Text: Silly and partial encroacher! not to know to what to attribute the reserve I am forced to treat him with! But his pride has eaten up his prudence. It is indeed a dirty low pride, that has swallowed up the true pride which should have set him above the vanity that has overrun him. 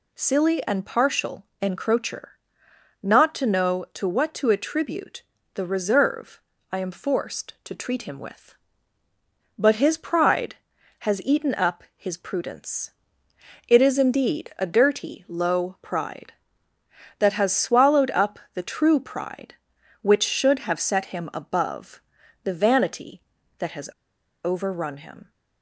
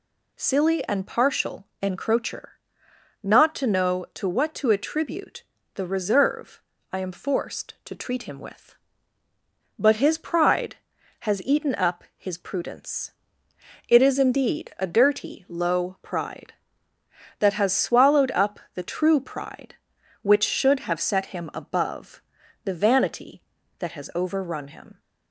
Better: second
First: pauses between "partial" and "encroacher"; slight; at 1.4 s; 0.16 s long // pauses between "attribute" and "the"; slight; at 5.2 s; 0.32 s long // pauses between "reserve" and "I"; slight; at 6.4 s; 0.30 s long // pauses between "up" and "the"; slight; at 18.3 s; 0.16 s long // pauses between "above" and "the"; at 22.0 s; 0.44 s long // pauses between "has" and "overrun"; noticeable; at 23.8 s; 0.55 s long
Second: pauses between "partial" and "encroacher"; slight; at 1.6 s; 0.15 s long // pauses between "attribute" and "the"; slight; at 5.4 s; 0.32 s long // pauses between "reserve" and "I"; slight; at 6.6 s; 0.30 s long // pauses between "up" and "the"; slight; at 18.5 s; 0.16 s long // pauses between "above" and "the"; at 22.2 s; 0.44 s long

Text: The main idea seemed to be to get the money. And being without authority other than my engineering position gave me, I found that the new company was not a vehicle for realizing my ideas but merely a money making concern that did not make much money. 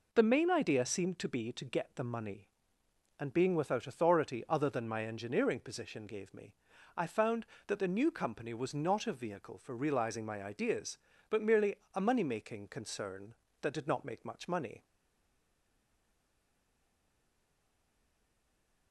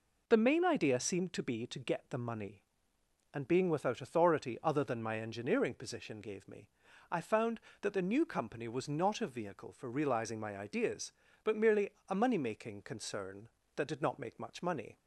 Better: second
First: pauses between "merely" and "a"; slight; at 11.7 s; 0.18 s long // stays silent after the last word; strong; from 14.8 s on; 4.1 s long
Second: pauses between "merely" and "a"; slight; at 11.8 s; 0.18 s long

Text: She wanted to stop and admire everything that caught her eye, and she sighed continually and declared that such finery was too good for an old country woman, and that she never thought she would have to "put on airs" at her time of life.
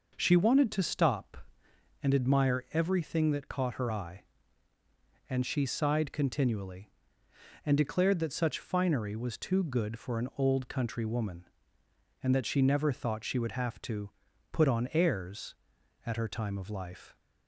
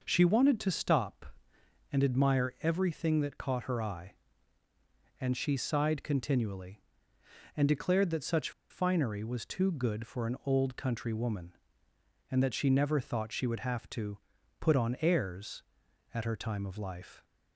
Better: first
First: pauses between "to" and "put"; at 14.0 s; 0.42 s long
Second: pauses between "such" and "finery"; slight; at 8.5 s; 0.20 s long // pauses between "to" and "put"; at 14.1 s; 0.42 s long

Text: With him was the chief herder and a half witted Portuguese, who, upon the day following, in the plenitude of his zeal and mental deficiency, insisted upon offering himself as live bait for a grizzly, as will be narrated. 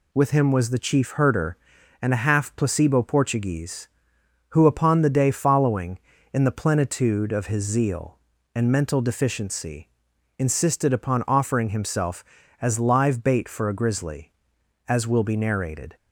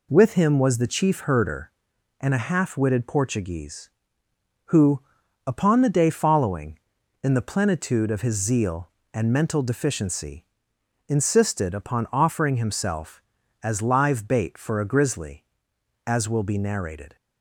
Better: second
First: says "placebo" for "witted"; at 2.5 s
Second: none

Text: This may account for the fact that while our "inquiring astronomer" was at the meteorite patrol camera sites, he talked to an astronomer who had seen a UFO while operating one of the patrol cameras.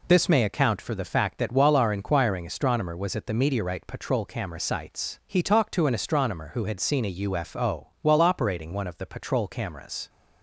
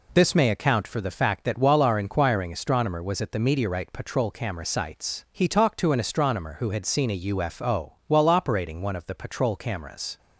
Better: neither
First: none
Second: none

